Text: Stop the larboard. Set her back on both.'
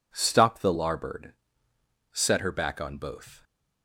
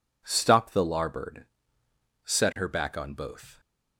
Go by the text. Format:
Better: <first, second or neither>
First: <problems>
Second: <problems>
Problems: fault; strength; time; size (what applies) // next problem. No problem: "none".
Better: neither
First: none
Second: none